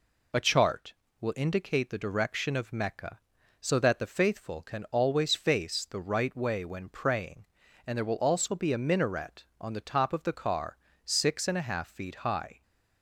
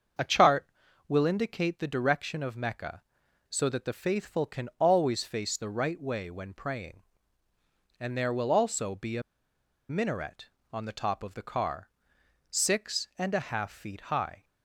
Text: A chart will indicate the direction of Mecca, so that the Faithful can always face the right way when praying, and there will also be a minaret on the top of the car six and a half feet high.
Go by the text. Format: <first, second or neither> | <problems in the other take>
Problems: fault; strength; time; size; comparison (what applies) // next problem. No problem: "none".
first | starts louder than the rest; until 1.6 s; 6.5 dB // pauses between "a" and "minaret"; noticeable; at 9.2 s; 0.67 s long // pauses between "car" and "six"; noticeable; at 11.8 s; 0.62 s long; slight in the first